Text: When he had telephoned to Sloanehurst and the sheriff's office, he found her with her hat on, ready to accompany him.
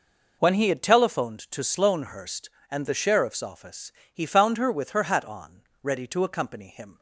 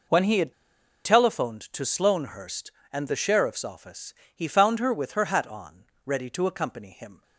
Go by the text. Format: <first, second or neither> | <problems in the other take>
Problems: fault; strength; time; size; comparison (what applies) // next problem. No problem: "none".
first | pauses between "had" and "telephoned"; noticeable; at 0.5 s; 0.53 s long